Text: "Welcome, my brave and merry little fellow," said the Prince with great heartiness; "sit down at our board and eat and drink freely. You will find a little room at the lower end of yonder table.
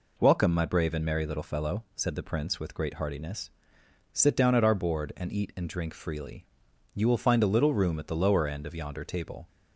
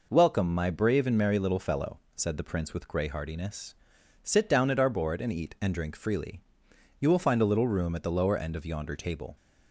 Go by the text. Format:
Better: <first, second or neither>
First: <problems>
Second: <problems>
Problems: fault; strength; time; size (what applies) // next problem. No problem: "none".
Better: first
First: none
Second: says "grey" for "great"; at 2.8 s